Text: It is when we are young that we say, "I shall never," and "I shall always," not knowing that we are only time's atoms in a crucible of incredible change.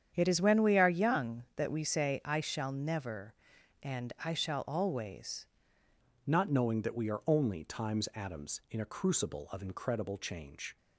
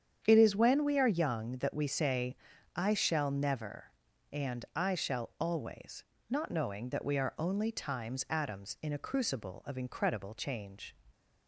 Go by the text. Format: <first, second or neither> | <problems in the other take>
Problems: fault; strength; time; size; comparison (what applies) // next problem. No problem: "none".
second | starts louder than the rest; strong; until 1.1 s; 8.5 dB; strong in the second // changes voice at "not"; from 6.2 s on; 4.5 s long